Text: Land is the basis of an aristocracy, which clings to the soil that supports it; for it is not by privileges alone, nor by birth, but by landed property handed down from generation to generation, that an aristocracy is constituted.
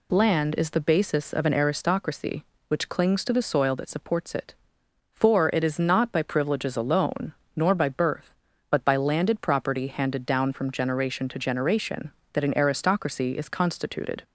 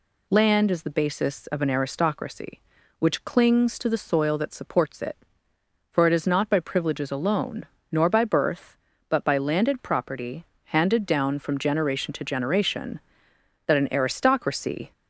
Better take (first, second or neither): first